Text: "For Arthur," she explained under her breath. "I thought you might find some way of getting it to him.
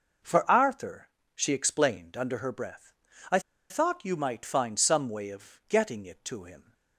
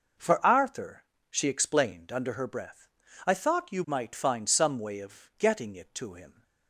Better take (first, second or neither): second